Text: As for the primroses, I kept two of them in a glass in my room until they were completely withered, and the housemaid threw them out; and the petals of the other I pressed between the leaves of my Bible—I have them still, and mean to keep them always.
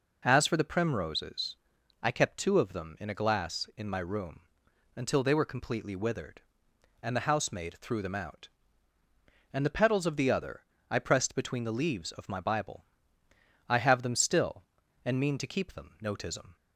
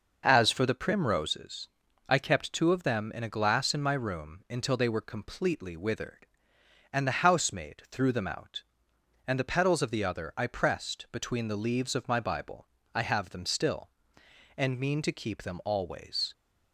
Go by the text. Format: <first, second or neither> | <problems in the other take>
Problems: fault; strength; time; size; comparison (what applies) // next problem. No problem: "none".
second | pauses between "room" and "until"; noticeable; at 4.4 s; 0.48 s long // pauses between "other" and "I"; slight; at 10.6 s; 0.26 s long // says "notism" for "always"; at 16.0 s